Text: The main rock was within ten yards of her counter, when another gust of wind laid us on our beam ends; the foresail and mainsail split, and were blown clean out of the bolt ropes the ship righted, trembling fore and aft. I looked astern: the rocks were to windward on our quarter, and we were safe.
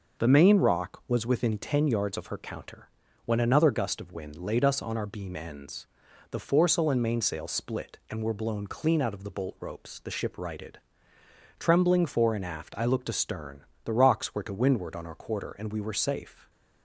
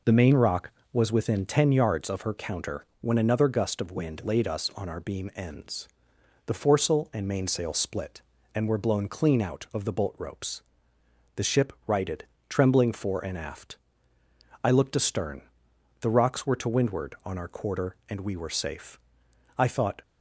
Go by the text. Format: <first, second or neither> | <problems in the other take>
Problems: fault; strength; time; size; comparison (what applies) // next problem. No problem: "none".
first | pauses between "ropes" and "the"; noticeable; at 10.6 s; 0.74 s long // goes on to say "I thought"; slight; from 19.5 s on; 0.44 s long